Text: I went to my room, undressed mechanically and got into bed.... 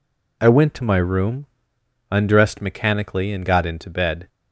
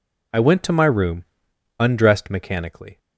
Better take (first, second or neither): first